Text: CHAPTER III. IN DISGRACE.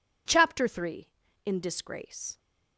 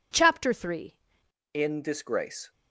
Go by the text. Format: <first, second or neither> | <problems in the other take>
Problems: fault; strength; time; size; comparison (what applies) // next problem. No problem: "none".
first | changes voice at "IN"; from 1.5 s on; 1.0 s long